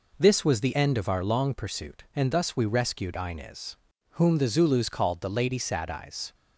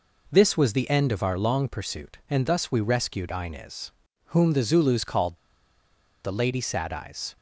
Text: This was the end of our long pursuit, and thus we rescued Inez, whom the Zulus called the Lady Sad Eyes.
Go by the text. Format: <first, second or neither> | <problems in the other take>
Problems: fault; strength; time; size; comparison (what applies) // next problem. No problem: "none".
first | pauses between "called" and "the"; noticeable; at 5.3 s; 0.87 s long